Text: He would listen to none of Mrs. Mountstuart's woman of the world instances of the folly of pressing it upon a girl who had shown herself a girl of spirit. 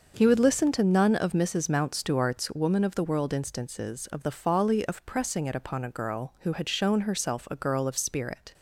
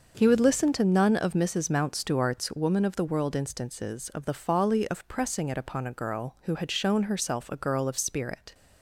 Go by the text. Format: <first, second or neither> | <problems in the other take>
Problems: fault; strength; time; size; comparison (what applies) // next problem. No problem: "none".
neither | starts louder than the rest; noticeable; the same in both